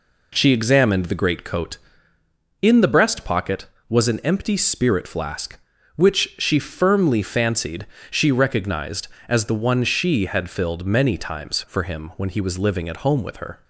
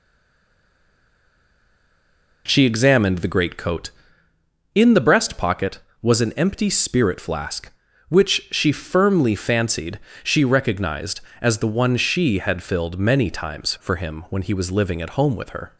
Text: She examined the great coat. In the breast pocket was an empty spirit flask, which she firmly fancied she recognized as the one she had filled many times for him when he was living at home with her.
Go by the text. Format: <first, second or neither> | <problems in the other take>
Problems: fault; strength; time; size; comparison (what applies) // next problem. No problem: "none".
first | stays silent before the first word; until 2.4 s; 2.4 s long // pauses between "fancied" and "she"; slight; at 9.9 s; 0.24 s long; slight in the first